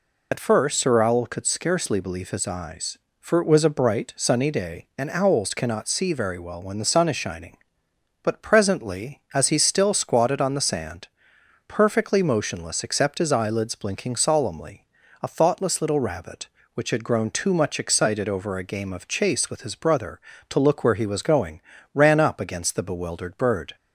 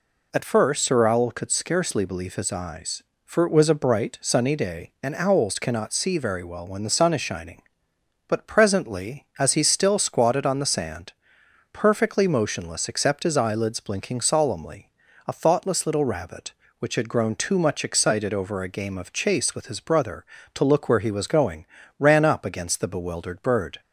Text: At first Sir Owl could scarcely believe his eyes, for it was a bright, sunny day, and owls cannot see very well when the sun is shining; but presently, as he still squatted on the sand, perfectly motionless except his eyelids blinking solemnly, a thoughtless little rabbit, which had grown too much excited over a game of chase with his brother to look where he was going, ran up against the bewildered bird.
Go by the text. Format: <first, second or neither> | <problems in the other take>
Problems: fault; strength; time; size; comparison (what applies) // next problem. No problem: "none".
second | loses the start of "At"; at 0.3 s; 40 ms